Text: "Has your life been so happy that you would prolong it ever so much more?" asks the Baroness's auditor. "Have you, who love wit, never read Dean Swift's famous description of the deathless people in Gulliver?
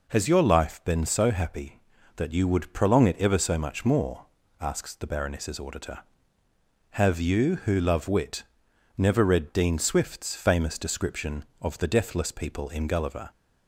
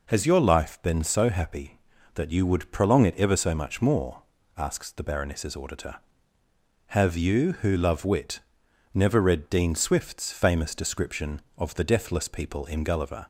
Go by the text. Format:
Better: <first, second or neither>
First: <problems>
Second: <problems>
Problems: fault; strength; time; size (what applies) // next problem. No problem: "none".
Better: neither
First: none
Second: none